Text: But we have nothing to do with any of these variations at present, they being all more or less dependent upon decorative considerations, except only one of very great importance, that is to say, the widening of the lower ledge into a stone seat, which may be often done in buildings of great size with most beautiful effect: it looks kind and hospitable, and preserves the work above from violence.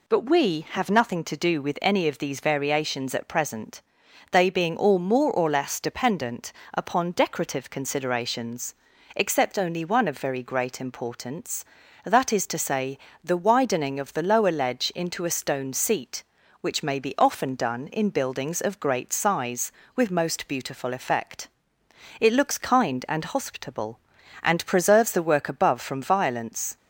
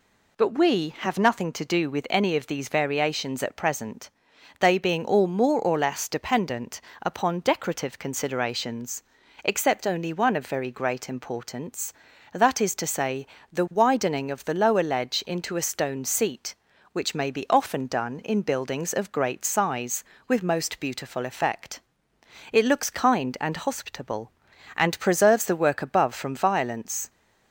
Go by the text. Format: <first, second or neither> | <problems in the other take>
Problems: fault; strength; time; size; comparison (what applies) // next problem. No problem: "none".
neither | pauses between "dependent" and "upon"; slight; the same in both